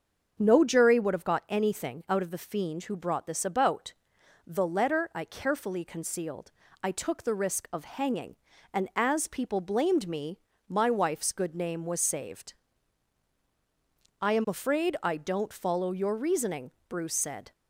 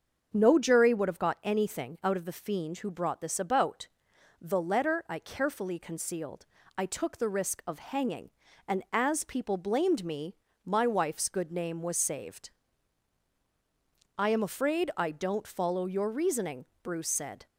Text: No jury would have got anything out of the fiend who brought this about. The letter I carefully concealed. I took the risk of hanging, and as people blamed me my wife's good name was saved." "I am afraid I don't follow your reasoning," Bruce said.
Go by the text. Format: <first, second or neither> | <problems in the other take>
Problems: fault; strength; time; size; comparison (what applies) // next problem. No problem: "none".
neither | starts louder than the rest; the same in both // pauses between "me" and "my"; slight; the same in both